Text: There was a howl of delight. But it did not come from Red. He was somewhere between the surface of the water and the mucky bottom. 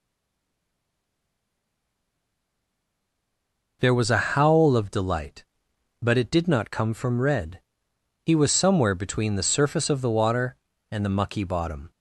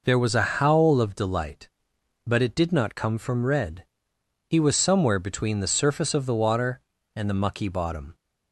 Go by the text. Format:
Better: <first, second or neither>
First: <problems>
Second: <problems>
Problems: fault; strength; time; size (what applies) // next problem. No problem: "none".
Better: second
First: stays silent before the first word; strong; until 3.8 s; 3.8 s long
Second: none